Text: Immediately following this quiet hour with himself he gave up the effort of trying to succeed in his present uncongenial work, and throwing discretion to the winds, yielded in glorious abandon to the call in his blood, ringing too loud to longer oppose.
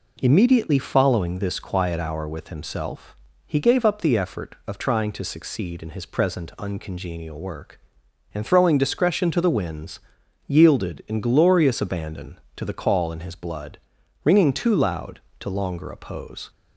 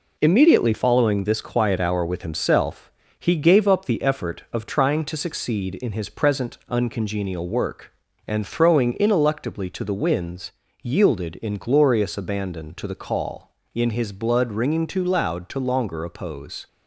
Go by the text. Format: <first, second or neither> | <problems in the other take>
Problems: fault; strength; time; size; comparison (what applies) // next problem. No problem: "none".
first | pauses between "himself" and "he"; slight; at 2.9 s; 0.28 s long; slight in the first // says "ineluctably" for "discretion"; at 8.9 s